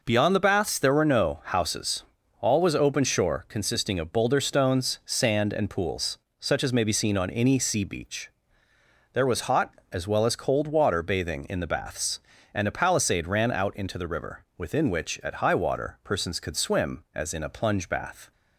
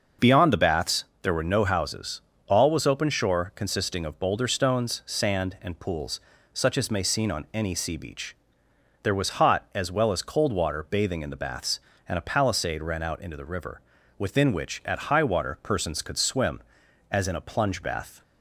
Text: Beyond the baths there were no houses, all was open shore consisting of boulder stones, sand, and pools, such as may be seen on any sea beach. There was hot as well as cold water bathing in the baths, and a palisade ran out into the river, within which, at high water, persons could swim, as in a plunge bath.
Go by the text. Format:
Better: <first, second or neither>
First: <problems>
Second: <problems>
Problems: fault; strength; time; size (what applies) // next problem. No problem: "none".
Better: first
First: none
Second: starts louder than the rest; until 1.3 s; 6 dB // pauses between "baths" and "there"; slight; at 1.0 s; 0.16 s long // skips "be"; at 7.0 s